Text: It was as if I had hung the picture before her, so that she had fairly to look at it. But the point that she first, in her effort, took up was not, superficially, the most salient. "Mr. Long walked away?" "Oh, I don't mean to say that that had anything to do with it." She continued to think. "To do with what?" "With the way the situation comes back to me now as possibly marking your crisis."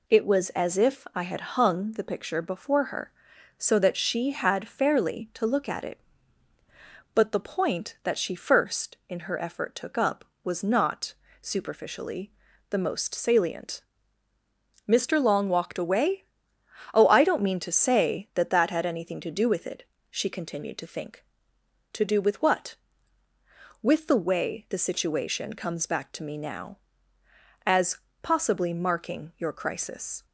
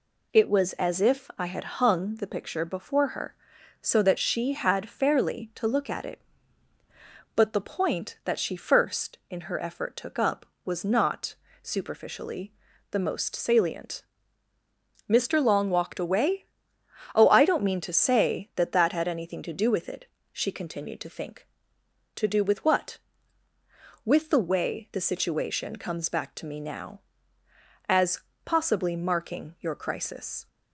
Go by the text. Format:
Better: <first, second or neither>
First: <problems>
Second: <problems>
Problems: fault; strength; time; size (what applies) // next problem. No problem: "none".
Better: neither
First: pauses between "as" and "possibly"; slight; at 27.9 s; 0.26 s long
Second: pauses between "as" and "possibly"; slight; at 28.1 s; 0.26 s long